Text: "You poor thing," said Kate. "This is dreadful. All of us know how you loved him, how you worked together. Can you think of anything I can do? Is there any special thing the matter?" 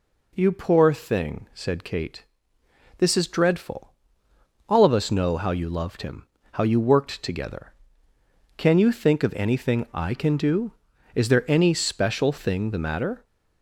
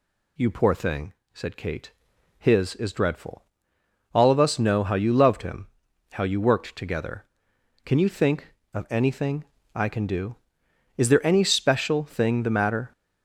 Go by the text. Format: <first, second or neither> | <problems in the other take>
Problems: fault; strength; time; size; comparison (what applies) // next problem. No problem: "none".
first | says "His" for "This"; at 2.3 s // pauses between "anything" and "I"; slight; at 9.4 s; 0.28 s long